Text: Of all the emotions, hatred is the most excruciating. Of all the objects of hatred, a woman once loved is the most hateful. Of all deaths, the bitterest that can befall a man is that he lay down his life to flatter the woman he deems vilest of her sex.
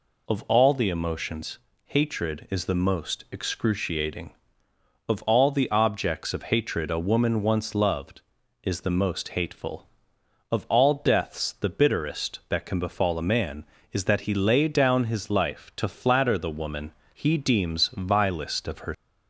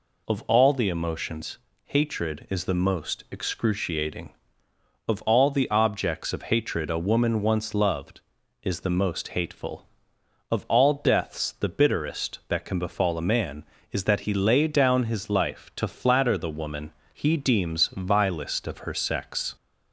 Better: second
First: pauses between "woman" and "he"; slight; at 16.9 s; 0.22 s long // stops before "sex"; at 18.9 s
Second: pauses between "woman" and "he"; slight; at 16.9 s; 0.22 s long

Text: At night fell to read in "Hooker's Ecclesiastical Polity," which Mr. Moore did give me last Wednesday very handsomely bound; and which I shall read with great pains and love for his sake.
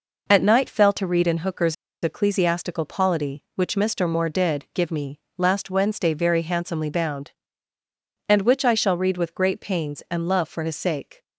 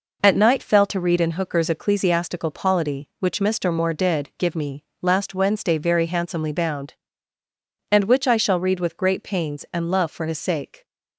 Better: second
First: pauses between "Hooker's" and "Ecclesiastical"; slight; at 1.7 s; 0.29 s long // pauses between "me" and "last"; slight; at 5.1 s; 0.20 s long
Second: pauses between "me" and "last"; slight; at 4.8 s; 0.20 s long

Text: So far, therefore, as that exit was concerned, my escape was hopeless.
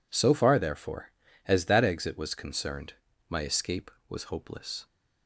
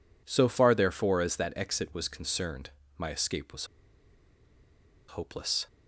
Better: first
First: none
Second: pauses between "was" and "hopeless"; strong; at 3.6 s; 1.4 s long

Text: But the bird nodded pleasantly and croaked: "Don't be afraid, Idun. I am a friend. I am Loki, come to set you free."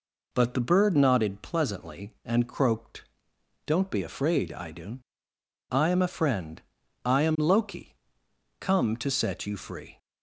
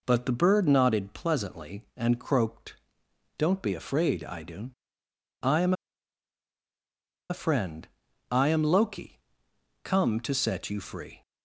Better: first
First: none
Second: pauses between "am" and "a"; strong; at 5.7 s; 1.5 s long

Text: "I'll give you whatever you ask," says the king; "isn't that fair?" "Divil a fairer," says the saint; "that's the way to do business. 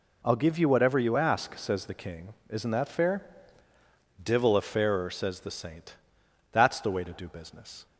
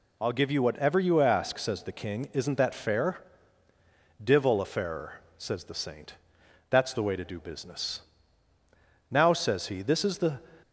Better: first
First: none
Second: goes on to say "Now says he this is the"; noticeable; from 9.1 s on; 1.2 s long

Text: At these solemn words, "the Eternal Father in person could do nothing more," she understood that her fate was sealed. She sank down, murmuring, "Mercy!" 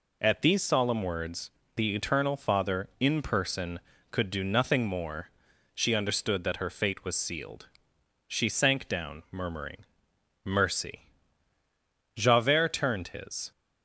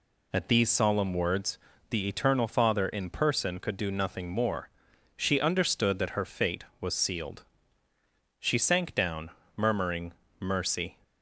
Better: second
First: goes on to say "Javert turned his"; from 12.1 s on; 1.3 s long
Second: none

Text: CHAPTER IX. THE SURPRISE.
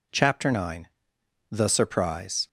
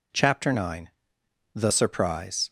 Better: neither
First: none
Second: none

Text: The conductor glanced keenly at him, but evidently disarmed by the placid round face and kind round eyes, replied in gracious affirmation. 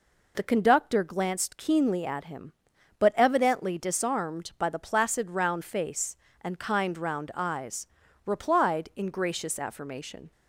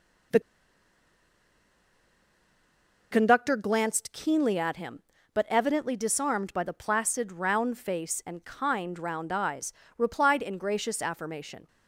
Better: first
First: none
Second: pauses between "The" and "conductor"; strong; at 0.4 s; 2.7 s long

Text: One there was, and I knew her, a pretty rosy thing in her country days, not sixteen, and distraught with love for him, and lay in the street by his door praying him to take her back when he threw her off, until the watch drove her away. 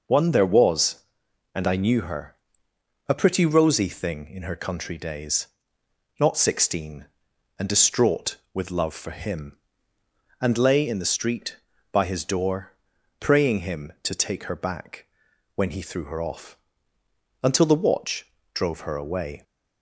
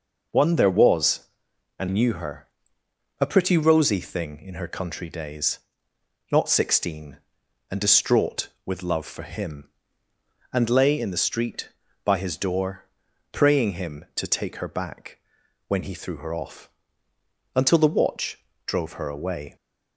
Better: first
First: pauses between "door" and "praying"; noticeable; at 12.7 s; 0.48 s long // pauses between "back" and "when"; noticeable; at 15.0 s; 0.50 s long // pauses between "watch" and "drove"; slight; at 18.2 s; 0.26 s long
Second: skips "I"; at 1.8 s // pauses between "door" and "praying"; noticeable; at 12.8 s; 0.48 s long // pauses between "back" and "when"; noticeable; at 15.1 s; 0.50 s long // pauses between "watch" and "drove"; slight; at 18.3 s; 0.26 s long

